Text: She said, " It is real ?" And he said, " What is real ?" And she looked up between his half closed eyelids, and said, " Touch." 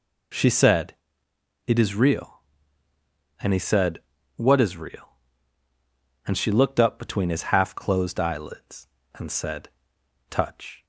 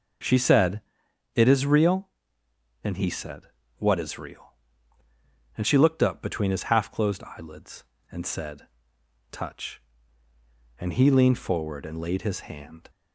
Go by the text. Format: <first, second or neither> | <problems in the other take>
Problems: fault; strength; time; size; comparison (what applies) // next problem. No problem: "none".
first | goes on to say "And he leaned forward and laid his hand"; strong; from 10.7 s on; 2.1 s long